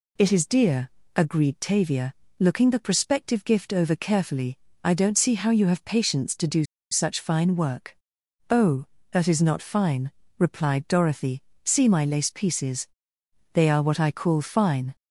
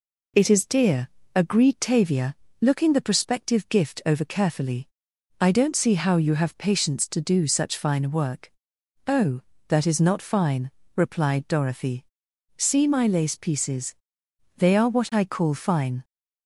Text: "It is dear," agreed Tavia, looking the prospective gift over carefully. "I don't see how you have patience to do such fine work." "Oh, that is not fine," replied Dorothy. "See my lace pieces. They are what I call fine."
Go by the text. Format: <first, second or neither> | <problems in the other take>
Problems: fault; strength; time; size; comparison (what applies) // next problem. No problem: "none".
second | pauses between "do" and "such"; slight; at 6.6 s; 0.27 s long